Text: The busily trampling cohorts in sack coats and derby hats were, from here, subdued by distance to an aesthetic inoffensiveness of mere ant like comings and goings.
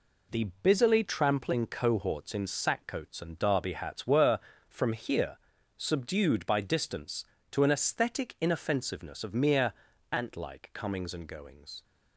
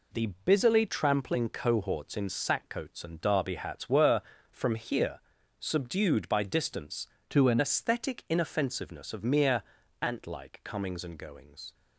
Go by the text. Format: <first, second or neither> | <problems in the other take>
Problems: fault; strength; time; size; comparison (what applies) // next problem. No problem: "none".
first | pauses between "The" and "busily"; slight; at 0.2 s; 0.16 s long; slight in the first // changes voice from "to" to "an"; from 7.2 to 7.6 s; 0.4 s long // pauses between "mere" and "ant"; at 9.6 s; 0.40 s long; also in the first